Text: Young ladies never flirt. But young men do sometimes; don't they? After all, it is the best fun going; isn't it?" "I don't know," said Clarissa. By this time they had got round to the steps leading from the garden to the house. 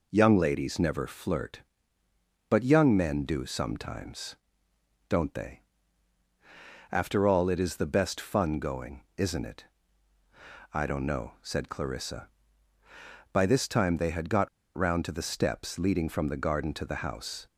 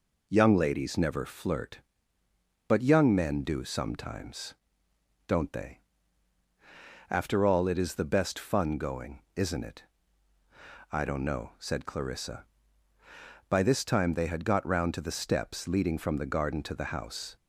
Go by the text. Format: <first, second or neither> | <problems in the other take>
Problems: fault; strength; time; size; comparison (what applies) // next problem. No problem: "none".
second | pauses between "got" and "round"; slight; at 14.4 s; 0.26 s long